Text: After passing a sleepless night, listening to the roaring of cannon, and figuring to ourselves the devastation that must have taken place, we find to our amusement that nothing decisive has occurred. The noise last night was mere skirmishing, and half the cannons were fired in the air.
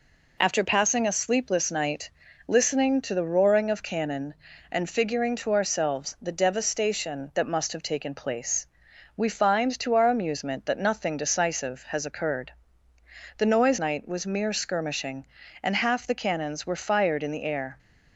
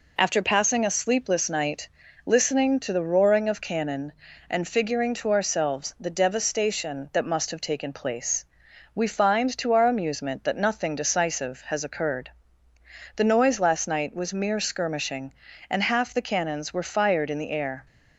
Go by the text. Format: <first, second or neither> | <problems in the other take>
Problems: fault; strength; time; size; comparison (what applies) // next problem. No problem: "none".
second | skips "last"; at 13.7 s